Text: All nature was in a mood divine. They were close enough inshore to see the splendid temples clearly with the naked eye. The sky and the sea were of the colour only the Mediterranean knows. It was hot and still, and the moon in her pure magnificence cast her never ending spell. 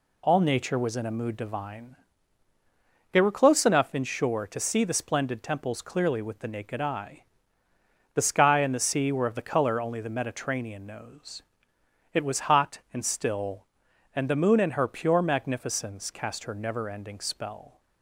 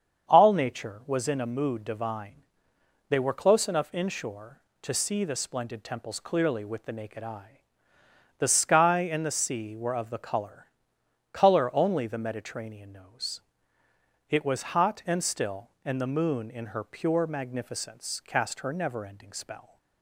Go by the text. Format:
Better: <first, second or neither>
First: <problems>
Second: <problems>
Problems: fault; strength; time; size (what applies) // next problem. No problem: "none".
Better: first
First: none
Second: starts louder than the rest; strong; until 1.3 s; 7.5 dB // says "colour" twice; at 11.3 s